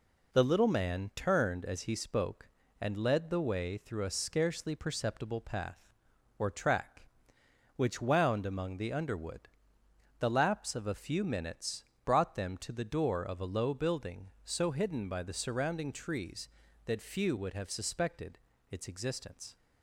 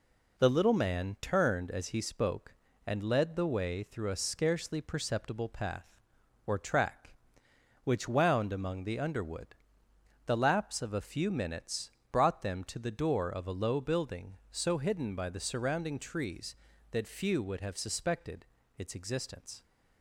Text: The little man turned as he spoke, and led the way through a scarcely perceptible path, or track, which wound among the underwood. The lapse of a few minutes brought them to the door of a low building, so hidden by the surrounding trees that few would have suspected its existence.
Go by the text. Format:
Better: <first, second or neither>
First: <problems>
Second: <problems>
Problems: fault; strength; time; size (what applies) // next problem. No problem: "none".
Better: neither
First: pauses between "minutes" and "brought"; slight; at 11.8 s; 0.22 s long // pauses between "suspected" and "its"; slight; at 18.3 s; 0.32 s long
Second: pauses between "minutes" and "brought"; slight; at 11.8 s; 0.22 s long // pauses between "suspected" and "its"; slight; at 18.4 s; 0.32 s long